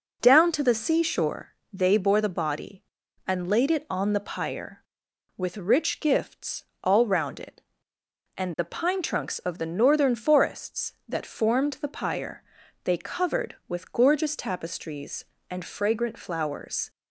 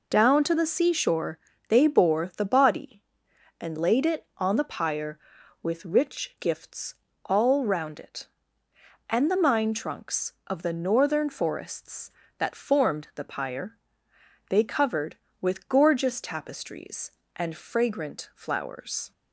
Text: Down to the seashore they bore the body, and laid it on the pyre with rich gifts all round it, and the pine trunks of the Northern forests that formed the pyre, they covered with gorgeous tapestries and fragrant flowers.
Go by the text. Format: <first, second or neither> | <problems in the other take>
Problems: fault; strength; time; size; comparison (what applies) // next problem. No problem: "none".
first | pauses between "seashore" and "they"; slight; at 1.3 s; 0.30 s long; slight in the first // pauses between "gifts" and "all"; slight; at 6.9 s; 0.30 s long; slight in the first // says "mine" for "pine"; at 9.3 s